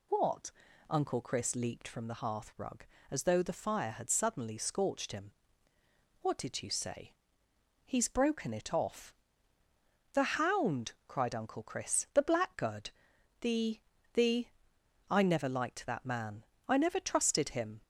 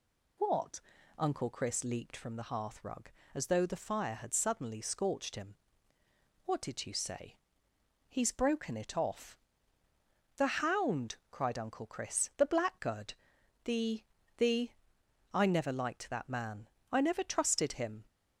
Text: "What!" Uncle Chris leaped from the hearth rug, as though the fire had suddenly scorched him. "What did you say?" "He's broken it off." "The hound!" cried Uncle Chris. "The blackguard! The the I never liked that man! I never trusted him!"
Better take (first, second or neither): neither